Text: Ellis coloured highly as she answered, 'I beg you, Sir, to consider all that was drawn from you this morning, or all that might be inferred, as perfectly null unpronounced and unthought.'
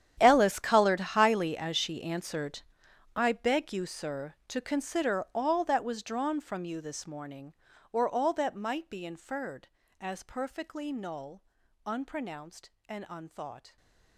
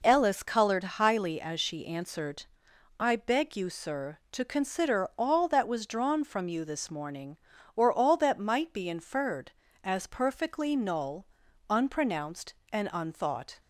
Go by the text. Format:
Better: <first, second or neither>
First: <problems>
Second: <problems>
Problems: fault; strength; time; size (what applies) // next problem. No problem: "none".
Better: second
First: gets quieter; strong; throughout; 18 dB // pauses between "null" and "unpronounced"; at 11.4 s; 0.42 s long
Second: pauses between "null" and "unpronounced"; at 11.2 s; 0.42 s long